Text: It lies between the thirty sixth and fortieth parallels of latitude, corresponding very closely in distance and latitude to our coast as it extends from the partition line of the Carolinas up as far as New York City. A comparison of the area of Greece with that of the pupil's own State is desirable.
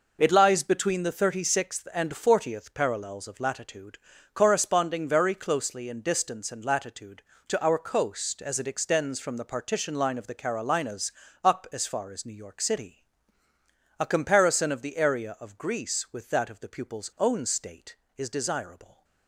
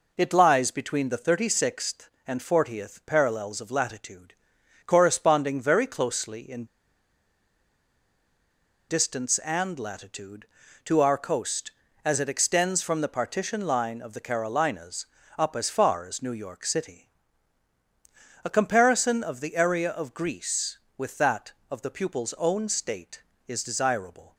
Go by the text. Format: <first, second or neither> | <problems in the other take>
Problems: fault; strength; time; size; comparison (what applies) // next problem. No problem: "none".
first | pauses between "in" and "distance"; strong; at 6.6 s; 2.2 s long // pauses between "Carolinas" and "up"; slight; at 15.0 s; 0.32 s long; slight in the first